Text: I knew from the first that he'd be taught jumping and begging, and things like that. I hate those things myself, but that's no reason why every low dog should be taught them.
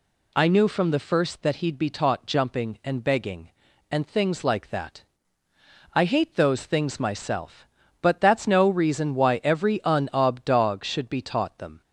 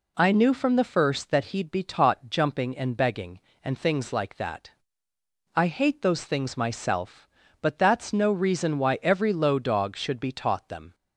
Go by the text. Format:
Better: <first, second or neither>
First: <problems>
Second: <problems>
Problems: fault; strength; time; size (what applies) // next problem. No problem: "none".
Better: second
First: says "unob" for "low"; at 9.8 s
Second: none